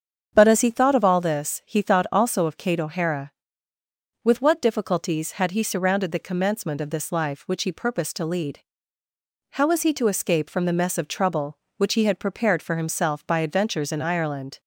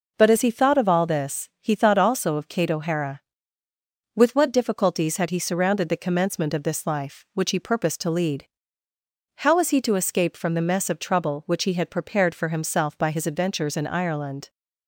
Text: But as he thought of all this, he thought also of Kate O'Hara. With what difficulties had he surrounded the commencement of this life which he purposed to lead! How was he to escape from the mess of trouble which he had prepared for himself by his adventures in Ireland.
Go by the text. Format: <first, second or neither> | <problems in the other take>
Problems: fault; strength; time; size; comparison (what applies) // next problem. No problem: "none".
second | starts louder than the rest; strong; until 1.3 s; 7.5 dB // skips "his"; at 13.3 s